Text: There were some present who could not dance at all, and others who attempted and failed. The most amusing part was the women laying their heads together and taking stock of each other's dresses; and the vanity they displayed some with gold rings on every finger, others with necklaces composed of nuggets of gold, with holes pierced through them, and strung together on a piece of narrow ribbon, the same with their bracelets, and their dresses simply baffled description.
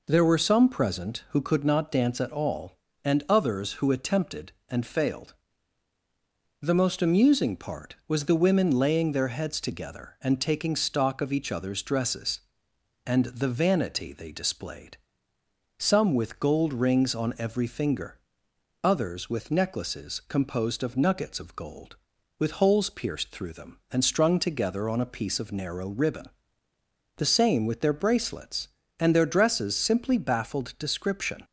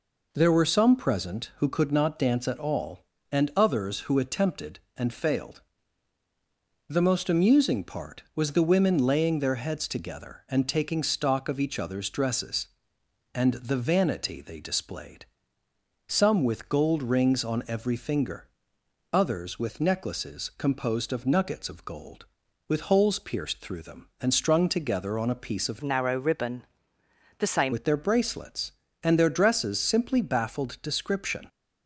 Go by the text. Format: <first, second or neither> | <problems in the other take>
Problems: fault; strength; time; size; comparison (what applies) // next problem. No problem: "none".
first | pauses between "displayed" and "some"; noticeable; at 15.2 s; 0.84 s long; noticeable in the first // changes voice from "narrow" to "same"; from 25.8 to 27.7 s; 1.9 s long